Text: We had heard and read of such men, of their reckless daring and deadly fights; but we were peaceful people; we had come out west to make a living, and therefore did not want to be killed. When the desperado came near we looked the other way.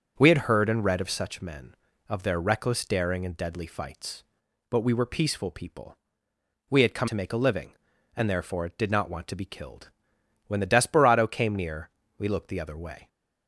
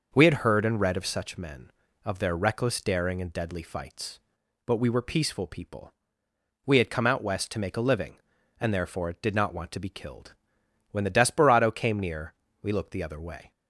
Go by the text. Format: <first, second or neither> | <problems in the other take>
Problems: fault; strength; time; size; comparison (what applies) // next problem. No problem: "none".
second | starts louder than the rest; until 1.1 s; 7 dB // skips "out west"; at 7.0 s // pauses between "near" and "we"; slight; at 11.8 s; 0.28 s long; slight in the second